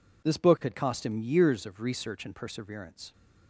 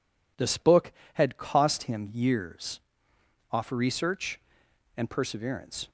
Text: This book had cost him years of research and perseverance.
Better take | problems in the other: first | says "off" for "of"; at 3.5 s

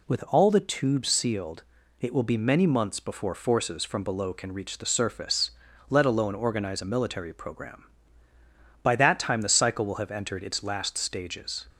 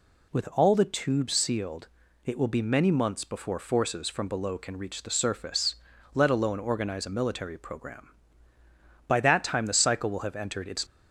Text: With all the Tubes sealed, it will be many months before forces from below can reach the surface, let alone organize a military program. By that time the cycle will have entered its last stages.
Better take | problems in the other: first | stops before "last stages"; at 10.8 s

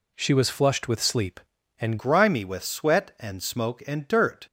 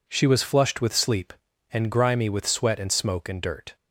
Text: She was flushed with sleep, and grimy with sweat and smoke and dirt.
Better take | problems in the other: second | changes voice at "grimy"; from 1.9 s on; 2.5 s long

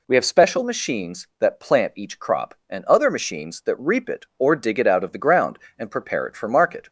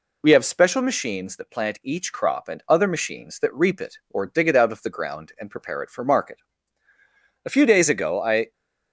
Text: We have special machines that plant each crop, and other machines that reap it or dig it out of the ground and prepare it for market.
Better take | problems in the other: first | goes on to say "A few days ago I"; noticeable; from 7.4 s on; 1.0 s long

